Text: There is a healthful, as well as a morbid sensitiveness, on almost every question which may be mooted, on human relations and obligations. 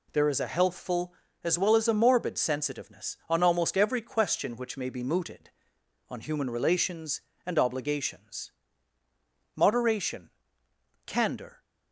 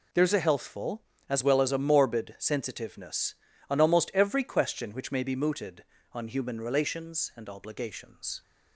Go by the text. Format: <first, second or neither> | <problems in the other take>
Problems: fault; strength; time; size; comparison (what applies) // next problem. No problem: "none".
second | goes on to say "Moderation candor"; strong; from 9.5 s on; 2.0 s long